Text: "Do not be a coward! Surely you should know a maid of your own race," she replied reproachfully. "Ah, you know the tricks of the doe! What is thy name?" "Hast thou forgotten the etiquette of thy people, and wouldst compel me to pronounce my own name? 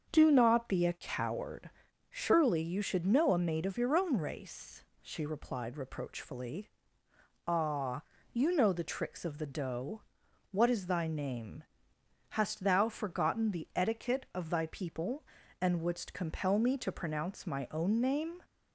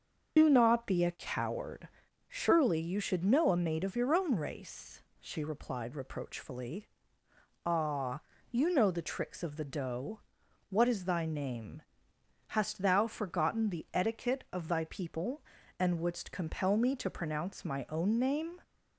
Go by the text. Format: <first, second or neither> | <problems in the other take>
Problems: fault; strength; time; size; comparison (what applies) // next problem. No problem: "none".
first | loses the start of "Do"; at 0.3 s; 105 ms // starts louder than the rest; until 1.3 s; 6.5 dB; also in the first